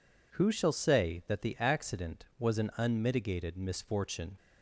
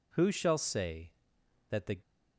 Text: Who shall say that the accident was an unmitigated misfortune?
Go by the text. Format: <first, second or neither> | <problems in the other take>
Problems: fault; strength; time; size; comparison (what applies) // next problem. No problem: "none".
first | stops before "accident was an unmitigated misfortune"; at 2.0 s